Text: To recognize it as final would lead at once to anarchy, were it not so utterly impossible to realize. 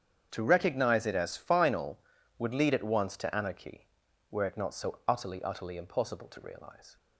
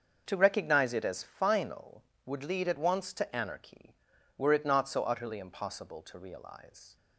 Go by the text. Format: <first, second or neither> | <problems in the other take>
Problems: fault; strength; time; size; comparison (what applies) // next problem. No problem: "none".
second | starts louder than the rest; strong; until 1.3 s; 8 dB; also in the second // says "utterly" twice; at 5.4 s